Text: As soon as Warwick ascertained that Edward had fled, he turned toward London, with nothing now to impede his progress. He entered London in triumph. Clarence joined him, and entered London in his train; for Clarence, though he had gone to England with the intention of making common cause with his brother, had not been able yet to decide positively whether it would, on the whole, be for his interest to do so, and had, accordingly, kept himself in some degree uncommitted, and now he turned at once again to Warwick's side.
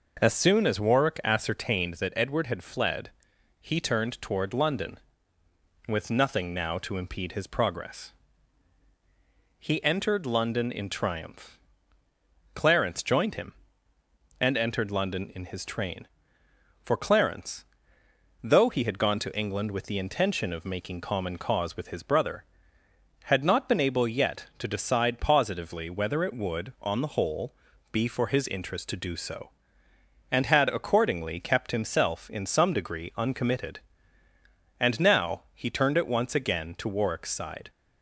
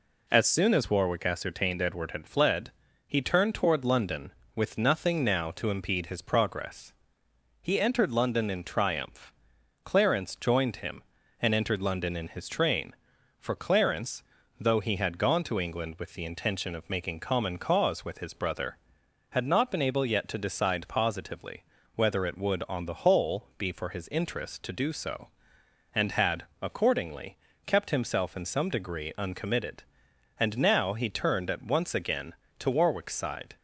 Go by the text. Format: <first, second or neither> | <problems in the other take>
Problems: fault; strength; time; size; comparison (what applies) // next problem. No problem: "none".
first | skips "that"; at 1.8 s // pauses between "positively" and "whether"; slight; at 21.6 s; 0.32 s long